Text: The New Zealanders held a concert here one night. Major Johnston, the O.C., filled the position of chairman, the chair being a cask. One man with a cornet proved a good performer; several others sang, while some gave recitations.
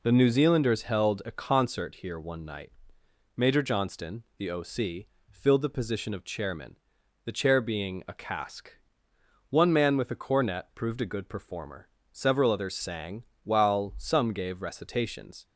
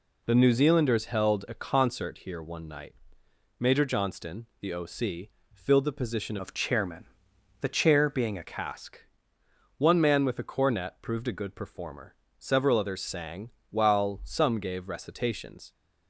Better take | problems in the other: first | changes voice from "of" to "a"; from 6.3 to 8.4 s; 2.1 s long

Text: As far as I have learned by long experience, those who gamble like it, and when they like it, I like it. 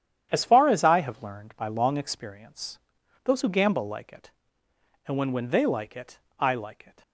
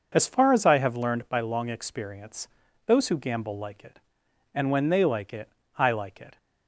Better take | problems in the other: second | starts louder than the rest; strong; until 1.3 s; 9.5 dB; also in the second // says "when" twice; at 5.3 s

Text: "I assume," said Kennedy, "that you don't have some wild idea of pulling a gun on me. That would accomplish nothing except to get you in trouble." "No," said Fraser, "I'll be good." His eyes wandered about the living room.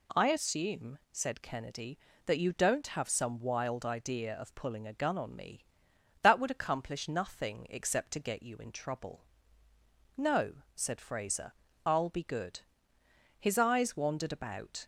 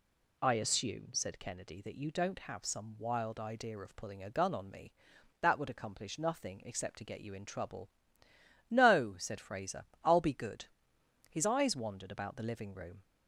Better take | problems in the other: second | stops before "the living room"; at 14.8 s

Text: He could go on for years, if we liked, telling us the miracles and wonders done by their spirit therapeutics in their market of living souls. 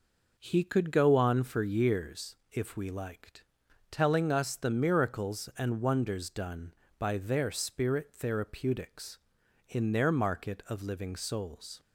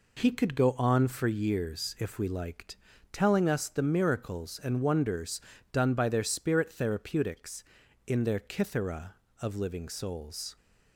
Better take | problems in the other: first | pauses between "wonders" and "done"; slight; at 5.3 s; 0.32 s long // says "kithera" for "market"; at 8.3 s

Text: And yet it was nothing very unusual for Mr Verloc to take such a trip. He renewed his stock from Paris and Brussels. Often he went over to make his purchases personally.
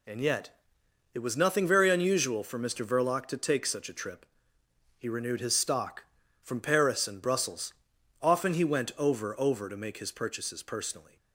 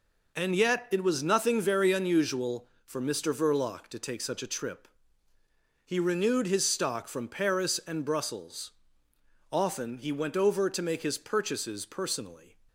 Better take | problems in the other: second | pauses between "yet" and "it"; noticeable; at 0.5 s; 0.64 s long // says "over" twice; at 9.3 s

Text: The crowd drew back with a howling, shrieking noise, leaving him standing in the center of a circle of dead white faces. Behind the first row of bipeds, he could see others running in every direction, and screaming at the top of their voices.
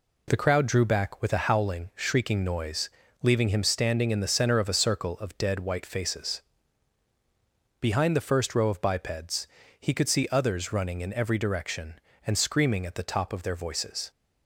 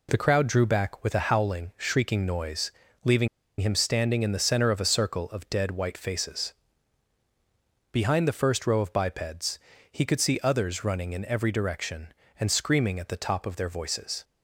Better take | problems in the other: first | pauses between "leaving" and "him"; slight; at 3.2 s; 0.31 s long

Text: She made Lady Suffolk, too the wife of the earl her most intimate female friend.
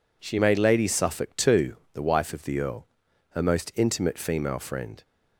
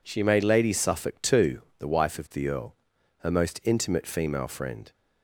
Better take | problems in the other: neither | pauses between "too" and "the"; slight; the same in both // pauses between "earl" and "her"; the same in both

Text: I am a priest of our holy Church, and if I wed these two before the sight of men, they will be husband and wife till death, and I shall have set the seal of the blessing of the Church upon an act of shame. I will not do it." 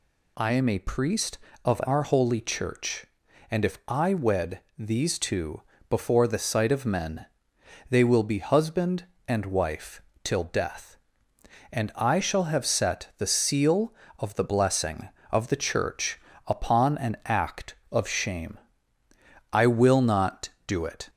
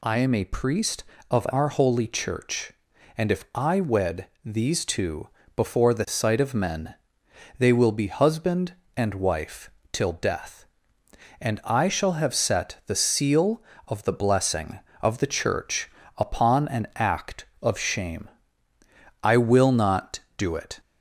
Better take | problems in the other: neither | pauses between "wed" and "these"; slight; the same in both // pauses between "two" and "before"; slight; the same in both // pauses between "wife" and "till"; slight; the same in both // pauses between "Church" and "upon"; slight; the same in both

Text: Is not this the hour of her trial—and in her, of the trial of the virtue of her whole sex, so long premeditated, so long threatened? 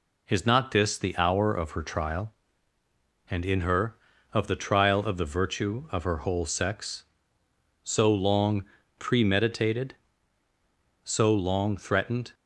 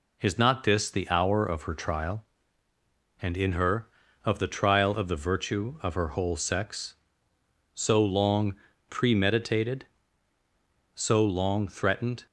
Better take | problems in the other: neither | pauses between "long" and "premeditated"; slight; the same in both

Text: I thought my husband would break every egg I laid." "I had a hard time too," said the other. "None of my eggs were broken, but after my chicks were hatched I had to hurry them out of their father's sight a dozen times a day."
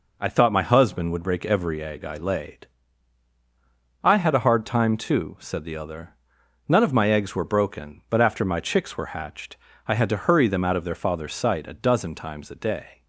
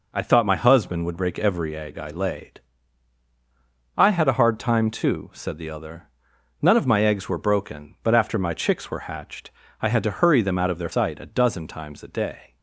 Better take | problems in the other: first | pauses between "hatched" and "I"; slight; at 9.5 s; 0.30 s long; slight in the first // skips "father's"; at 10.9 s

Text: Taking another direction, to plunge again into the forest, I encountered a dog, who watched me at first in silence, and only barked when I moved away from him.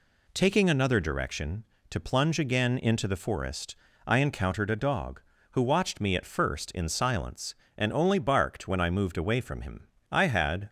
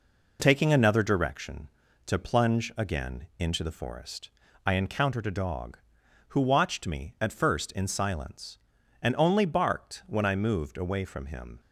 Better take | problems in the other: second | goes on to say "I had"; from 10.1 s on; 0.58 s long

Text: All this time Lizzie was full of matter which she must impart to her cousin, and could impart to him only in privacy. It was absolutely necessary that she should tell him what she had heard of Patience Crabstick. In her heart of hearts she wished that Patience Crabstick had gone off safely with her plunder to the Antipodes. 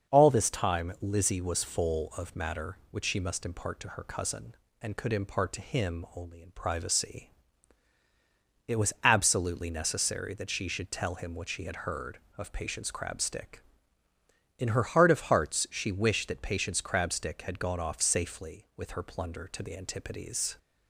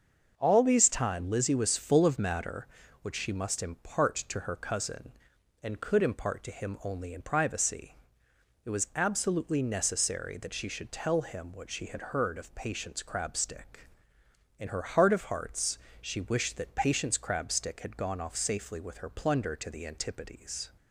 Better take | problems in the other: first | starts louder than the rest; until 1.3 s; 6 dB; also in the first // says "these" for "this"; at 0.6 s // pauses between "hearts" and "she"; slight; at 15.7 s; 0.24 s long

